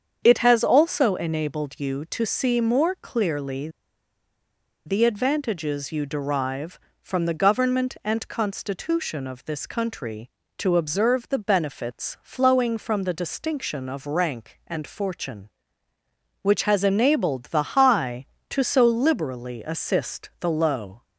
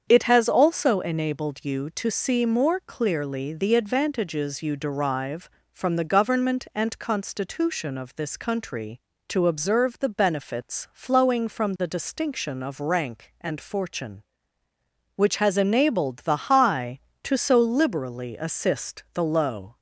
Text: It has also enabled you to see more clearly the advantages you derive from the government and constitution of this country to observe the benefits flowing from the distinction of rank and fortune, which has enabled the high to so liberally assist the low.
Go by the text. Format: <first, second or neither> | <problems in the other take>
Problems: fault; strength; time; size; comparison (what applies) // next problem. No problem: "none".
second | starts louder than the rest; strong; until 1.2 s; 7.5 dB; strong in the second // pauses between "clearly" and "the"; at 3.6 s; 1.1 s long